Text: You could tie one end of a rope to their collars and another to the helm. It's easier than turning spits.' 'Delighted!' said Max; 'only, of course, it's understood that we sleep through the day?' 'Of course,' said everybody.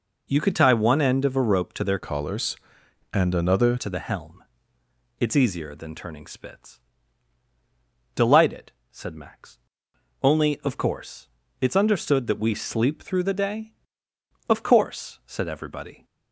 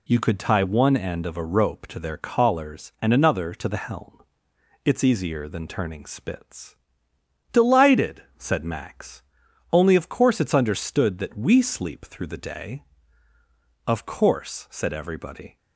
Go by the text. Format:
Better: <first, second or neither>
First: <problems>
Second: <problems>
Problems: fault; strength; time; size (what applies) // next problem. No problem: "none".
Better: second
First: changes voice from "collars" to "another"; from 1.9 to 3.7 s; 1.8 s long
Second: none